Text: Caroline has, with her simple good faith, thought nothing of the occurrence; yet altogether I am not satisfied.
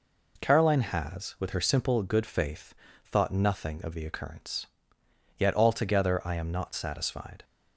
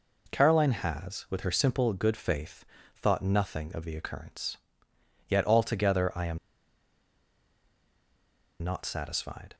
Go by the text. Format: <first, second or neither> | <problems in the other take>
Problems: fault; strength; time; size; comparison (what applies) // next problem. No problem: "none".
first | pauses between "am" and "not"; strong; at 6.3 s; 2.2 s long